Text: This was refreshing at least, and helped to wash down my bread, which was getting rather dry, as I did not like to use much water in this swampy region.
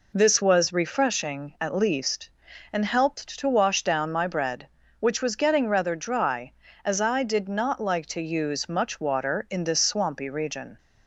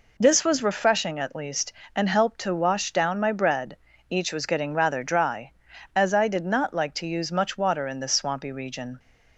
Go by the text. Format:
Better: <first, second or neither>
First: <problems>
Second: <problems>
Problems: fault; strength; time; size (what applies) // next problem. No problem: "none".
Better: first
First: none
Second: says "each" for "which"; at 4.0 s